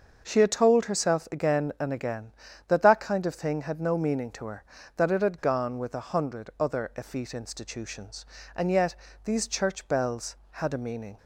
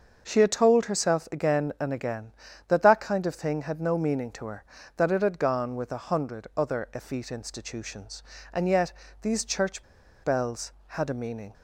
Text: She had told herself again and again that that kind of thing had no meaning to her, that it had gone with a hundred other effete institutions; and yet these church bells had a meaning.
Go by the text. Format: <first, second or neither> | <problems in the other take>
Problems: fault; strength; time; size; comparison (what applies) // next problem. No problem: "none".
first | starts louder than the rest; until 1.2 s; 6.5 dB; also in the first // pauses between "yet" and "these"; slight; at 8.9 s; 0.26 s long; slight in the first // pauses between "church" and "bells"; at 9.8 s; 0.39 s long